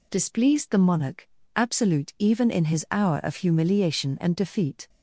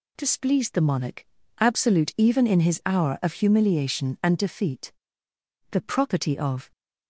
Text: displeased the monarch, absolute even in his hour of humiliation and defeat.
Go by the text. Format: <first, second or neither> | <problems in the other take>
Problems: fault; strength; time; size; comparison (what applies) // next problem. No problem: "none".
first | goes on to say "The property of"; noticeable; from 5.7 s on; 1.0 s long